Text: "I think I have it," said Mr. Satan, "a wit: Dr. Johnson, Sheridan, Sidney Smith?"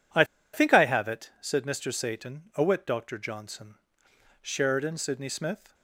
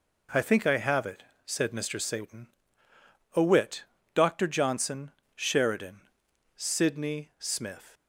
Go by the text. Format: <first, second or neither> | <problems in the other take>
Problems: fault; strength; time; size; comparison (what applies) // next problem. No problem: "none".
second | pauses between "I" and "think"; slight; at 0.2 s; 0.28 s long